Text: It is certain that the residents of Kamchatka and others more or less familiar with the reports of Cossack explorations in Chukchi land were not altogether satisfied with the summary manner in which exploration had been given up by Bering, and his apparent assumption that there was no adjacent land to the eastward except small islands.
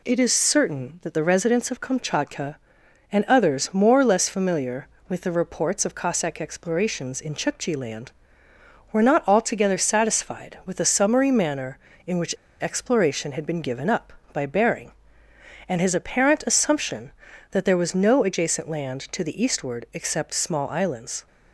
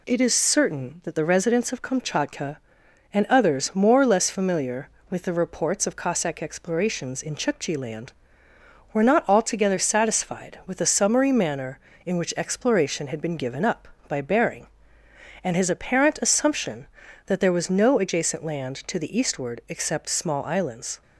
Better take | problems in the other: second | pauses between "which" and "exploration"; slight; at 12.3 s; 0.25 s long

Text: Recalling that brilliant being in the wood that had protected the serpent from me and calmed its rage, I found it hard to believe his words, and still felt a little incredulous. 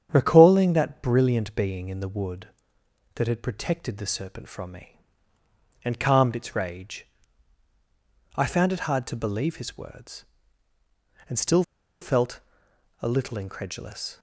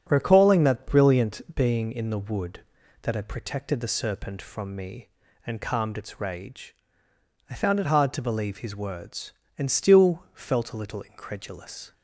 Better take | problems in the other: second | starts louder than the rest; strong; until 1.1 s; 8.5 dB; strong in the second // pauses between "still" and "felt"; at 11.6 s; 0.39 s long // pauses between "felt" and "a"; noticeable; at 12.3 s; 0.64 s long

